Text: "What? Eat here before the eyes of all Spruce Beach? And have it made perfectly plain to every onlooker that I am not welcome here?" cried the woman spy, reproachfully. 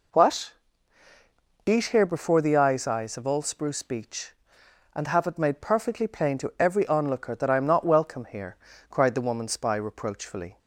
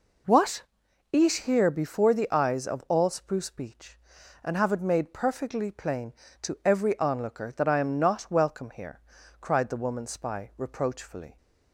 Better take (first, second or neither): second